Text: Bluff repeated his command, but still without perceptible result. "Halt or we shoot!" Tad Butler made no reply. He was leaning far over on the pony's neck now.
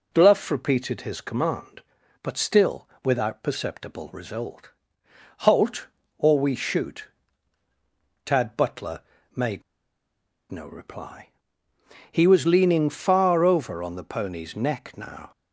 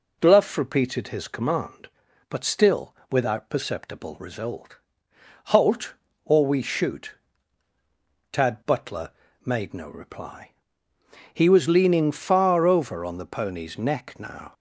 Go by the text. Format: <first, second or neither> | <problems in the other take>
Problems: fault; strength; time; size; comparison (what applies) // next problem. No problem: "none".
second | pauses between "still" and "without"; slight; at 2.8 s; 0.16 s long; slight in the second // pauses between "Butler" and "made"; slight; at 8.9 s; 0.34 s long; slight in the second // pauses between "made" and "no"; noticeable; at 9.6 s; 0.88 s long